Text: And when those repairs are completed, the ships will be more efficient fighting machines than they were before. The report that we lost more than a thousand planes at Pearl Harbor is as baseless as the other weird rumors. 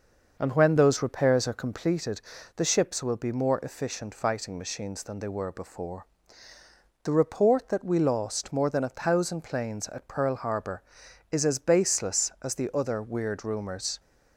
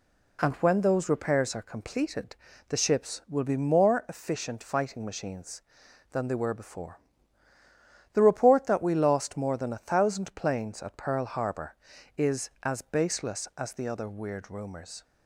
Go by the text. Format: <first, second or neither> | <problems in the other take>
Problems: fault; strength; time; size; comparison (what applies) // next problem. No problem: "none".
second | starts louder than the rest; noticeable; until 1.9 s; 6 dB